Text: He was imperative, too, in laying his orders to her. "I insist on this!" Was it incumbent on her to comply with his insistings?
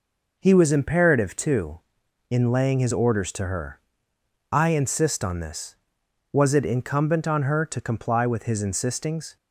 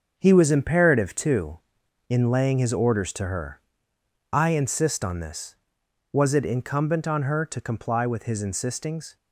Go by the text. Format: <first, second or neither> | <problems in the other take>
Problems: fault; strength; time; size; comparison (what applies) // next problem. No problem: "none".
first | gets quieter; strong; throughout; 8 dB